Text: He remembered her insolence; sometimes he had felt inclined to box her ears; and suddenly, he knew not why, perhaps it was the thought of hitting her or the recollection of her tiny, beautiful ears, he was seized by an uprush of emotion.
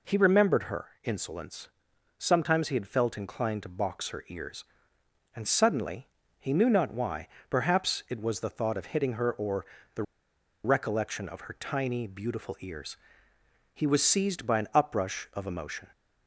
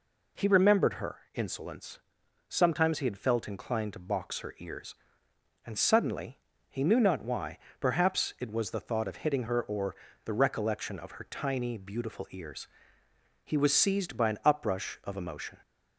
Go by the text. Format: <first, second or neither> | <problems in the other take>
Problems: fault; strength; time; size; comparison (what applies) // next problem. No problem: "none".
second | pauses between "or" and "the"; slight; at 9.6 s; 0.30 s long; slight in the second // pauses between "the" and "recollection"; noticeable; at 10.0 s; 0.60 s long